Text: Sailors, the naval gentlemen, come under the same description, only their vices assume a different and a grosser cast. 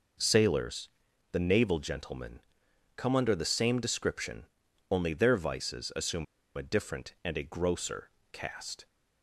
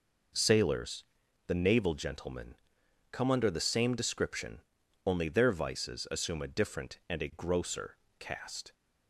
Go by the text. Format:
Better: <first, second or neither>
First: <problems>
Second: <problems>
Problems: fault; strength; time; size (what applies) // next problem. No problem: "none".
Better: second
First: pauses between "assume" and "a"; slight; at 6.2 s; 0.31 s long // pauses between "grosser" and "cast"; slight; at 8.0 s; 0.24 s long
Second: pauses between "grosser" and "cast"; slight; at 7.9 s; 0.24 s long